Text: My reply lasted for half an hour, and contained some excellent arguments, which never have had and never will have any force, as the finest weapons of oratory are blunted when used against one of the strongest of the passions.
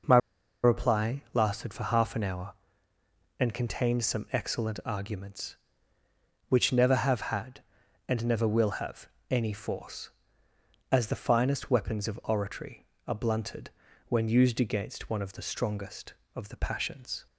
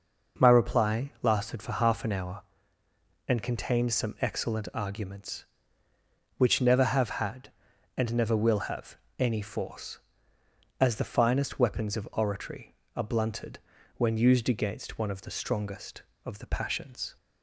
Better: second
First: pauses between "My" and "reply"; at 0.1 s; 0.45 s long // pauses between "have" and "any"; slight; at 9.0 s; 0.22 s long // pauses between "blunted" and "when"; at 13.6 s; 0.40 s long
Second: pauses between "have" and "any"; slight; at 8.9 s; 0.22 s long // pauses between "blunted" and "when"; at 13.5 s; 0.40 s long

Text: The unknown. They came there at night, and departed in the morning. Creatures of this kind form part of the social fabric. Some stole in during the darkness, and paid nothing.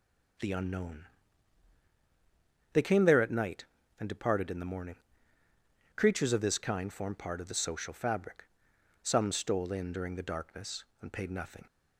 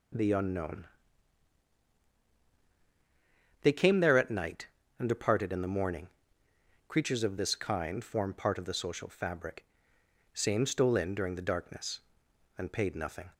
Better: first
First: none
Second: says "Same" for "Some"; at 10.3 s

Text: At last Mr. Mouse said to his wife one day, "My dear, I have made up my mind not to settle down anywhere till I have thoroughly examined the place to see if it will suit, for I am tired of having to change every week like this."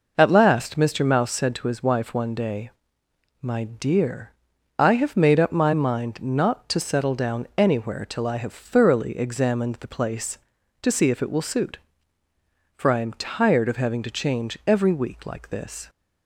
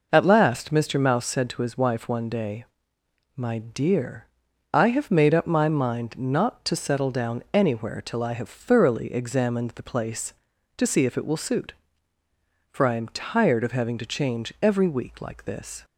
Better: neither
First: none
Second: none

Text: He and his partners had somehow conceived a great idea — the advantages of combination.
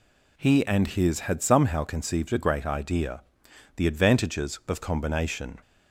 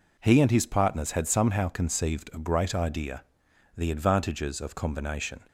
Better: second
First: skips "partners"; at 1.2 s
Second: none

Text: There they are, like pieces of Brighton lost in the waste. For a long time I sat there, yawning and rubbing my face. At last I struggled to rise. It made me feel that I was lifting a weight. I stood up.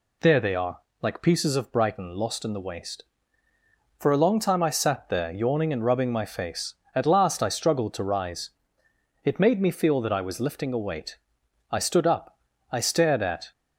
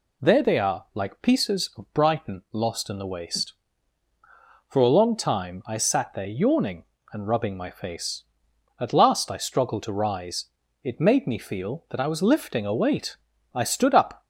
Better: second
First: goes on to say "I stared at"; noticeable; from 12.7 s on; 0.80 s long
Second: none

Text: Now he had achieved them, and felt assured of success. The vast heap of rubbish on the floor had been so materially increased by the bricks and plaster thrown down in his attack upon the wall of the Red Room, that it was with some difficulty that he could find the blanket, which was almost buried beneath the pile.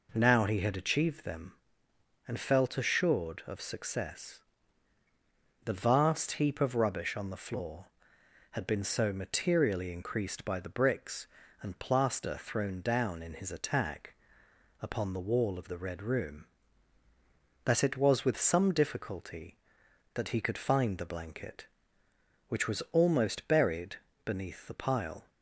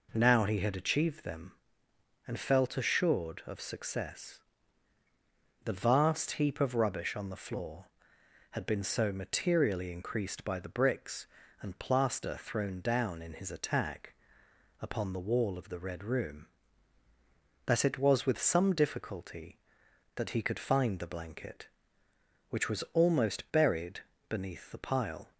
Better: neither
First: pauses between "attack" and "upon"; noticeable; at 14.1 s; 0.68 s long // pauses between "buried" and "beneath"; slight; at 23.9 s; 0.28 s long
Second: pauses between "attack" and "upon"; noticeable; at 14.1 s; 0.68 s long // pauses between "buried" and "beneath"; slight; at 24.0 s; 0.28 s long

